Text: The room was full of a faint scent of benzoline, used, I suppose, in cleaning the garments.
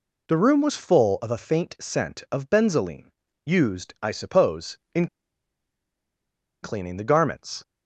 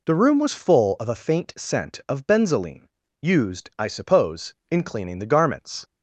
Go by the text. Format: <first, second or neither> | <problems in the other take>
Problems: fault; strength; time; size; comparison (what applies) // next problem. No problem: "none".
second | pauses between "in" and "cleaning"; strong; at 5.0 s; 1.5 s long